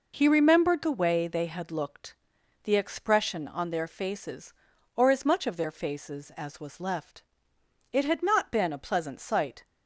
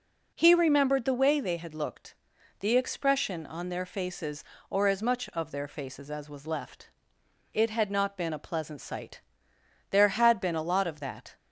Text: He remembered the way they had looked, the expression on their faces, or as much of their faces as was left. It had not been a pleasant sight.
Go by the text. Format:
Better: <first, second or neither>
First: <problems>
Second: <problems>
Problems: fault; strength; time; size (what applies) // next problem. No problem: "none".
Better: first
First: none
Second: goes on to say "There had been a lot of that"; from 9.8 s on; 1.4 s long